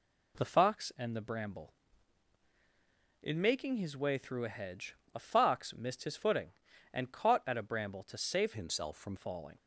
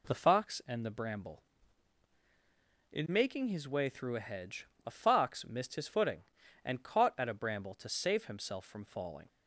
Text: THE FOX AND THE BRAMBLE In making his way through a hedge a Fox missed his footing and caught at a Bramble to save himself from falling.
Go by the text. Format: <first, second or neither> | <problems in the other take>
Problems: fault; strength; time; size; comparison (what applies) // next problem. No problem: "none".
second | pauses between "hedge" and "a"; slight; at 4.9 s; 0.20 s long; slight in the second // changes voice from "himself" to "from"; from 8.5 to 9.1 s; 0.6 s long